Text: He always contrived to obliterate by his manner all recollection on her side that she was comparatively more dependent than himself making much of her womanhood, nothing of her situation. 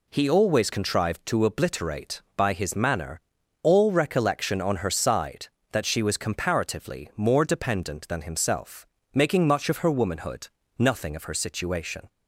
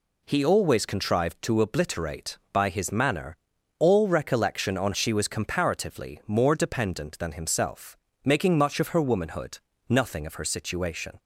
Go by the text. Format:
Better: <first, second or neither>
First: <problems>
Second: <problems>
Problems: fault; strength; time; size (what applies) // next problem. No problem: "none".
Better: first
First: pauses between "manner" and "all"; at 3.1 s; 0.42 s long // pauses between "himself" and "making"; slight; at 8.8 s; 0.28 s long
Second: pauses between "manner" and "all"; at 3.3 s; 0.42 s long // skips "her side that"; at 4.9 s // pauses between "himself" and "making"; slight; at 7.9 s; 0.28 s long